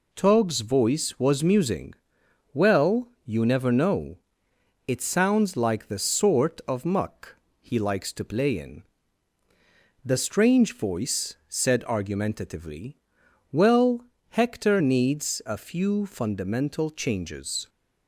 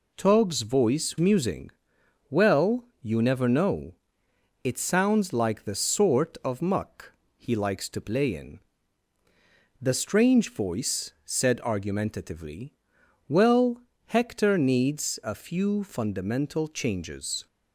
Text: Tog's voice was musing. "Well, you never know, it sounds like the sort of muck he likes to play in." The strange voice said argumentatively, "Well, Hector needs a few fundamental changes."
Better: first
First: pauses between "muck" and "he"; slight; at 7.3 s; 0.26 s long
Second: skips "was"; at 1.1 s // pauses between "muck" and "he"; slight; at 7.1 s; 0.26 s long

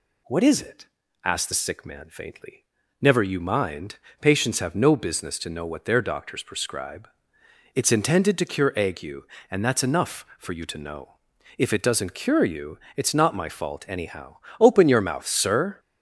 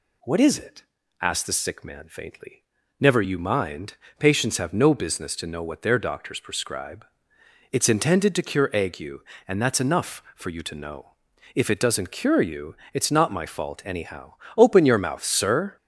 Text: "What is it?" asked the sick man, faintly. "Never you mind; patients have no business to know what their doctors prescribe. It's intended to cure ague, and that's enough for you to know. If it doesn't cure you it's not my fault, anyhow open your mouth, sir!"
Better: neither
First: pauses between "you" and "it's"; slight; at 12.7 s; 0.18 s long // pauses between "anyhow" and "open"; slight; at 14.3 s; 0.22 s long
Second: pauses between "you" and "it's"; slight; at 12.7 s; 0.18 s long // pauses between "anyhow" and "open"; slight; at 14.3 s; 0.22 s long

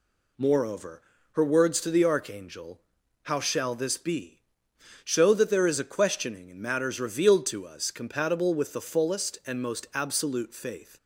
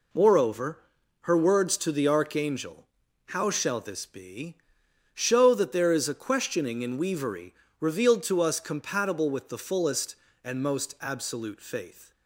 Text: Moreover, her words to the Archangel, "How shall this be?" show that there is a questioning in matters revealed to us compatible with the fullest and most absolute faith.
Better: first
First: none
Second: says "weavery" for "matters"; at 6.9 s

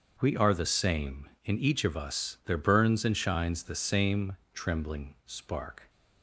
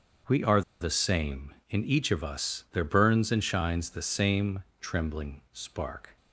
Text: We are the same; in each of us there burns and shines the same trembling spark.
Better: first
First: starts louder than the rest; until 1.2 s; 6.5 dB // pauses between "same" and "trembling"; slight; at 4.3 s; 0.16 s long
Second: starts louder than the rest; until 1.4 s; 6.5 dB // pauses between "are" and "the"; slight; at 0.6 s; 0.20 s long // pauses between "same" and "trembling"; slight; at 4.6 s; 0.16 s long

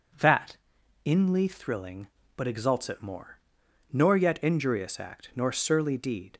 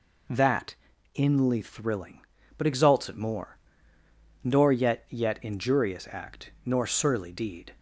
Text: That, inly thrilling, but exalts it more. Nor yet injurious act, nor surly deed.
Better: first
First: none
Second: says "yet" twice; at 5.0 s

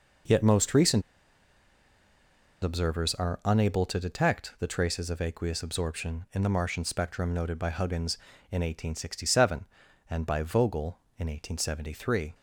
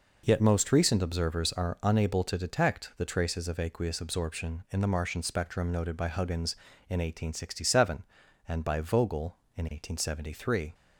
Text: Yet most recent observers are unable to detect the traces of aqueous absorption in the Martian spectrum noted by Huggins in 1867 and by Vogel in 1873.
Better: second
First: pauses between "recent" and "observers"; strong; at 1.0 s; 1.6 s long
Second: none

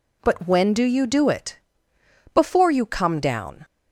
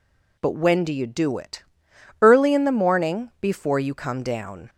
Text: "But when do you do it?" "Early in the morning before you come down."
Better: second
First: skips "Early in the morning"; at 1.9 s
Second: none

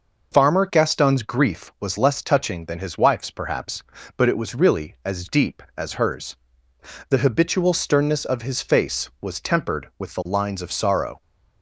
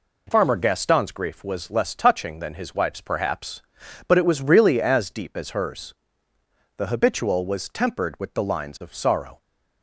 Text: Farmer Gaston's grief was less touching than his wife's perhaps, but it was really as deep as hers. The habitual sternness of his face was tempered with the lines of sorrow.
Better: first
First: none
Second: skips "sternness of his face"; at 7.4 s

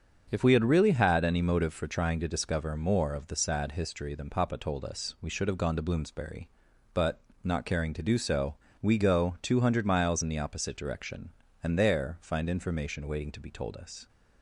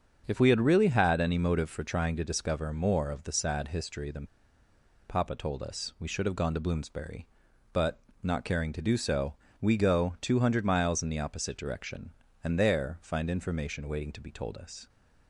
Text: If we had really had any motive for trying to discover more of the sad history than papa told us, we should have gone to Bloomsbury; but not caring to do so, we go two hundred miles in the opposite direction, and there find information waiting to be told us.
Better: first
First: starts louder than the rest; until 1.3 s; 7 dB // pauses between "but" and "not"; slight; at 7.2 s; 0.24 s long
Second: starts louder than the rest; until 1.2 s; 7 dB // pauses between "than" and "papa"; noticeable; at 4.2 s; 0.84 s long // pauses between "but" and "not"; slight; at 8.0 s; 0.24 s long

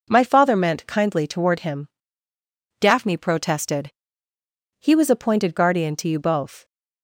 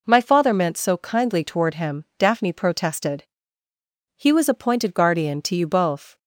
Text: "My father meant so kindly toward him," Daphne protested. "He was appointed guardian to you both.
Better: second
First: skips "so"; at 0.8 s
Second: none

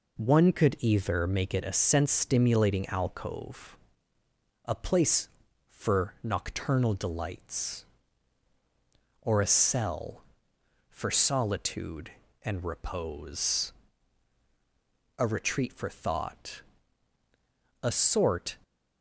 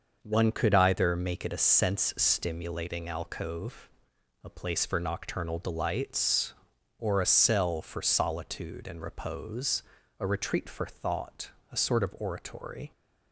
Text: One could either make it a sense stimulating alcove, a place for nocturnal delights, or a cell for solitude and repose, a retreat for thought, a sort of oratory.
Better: second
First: stops before "of oratory"; at 18.6 s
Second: none

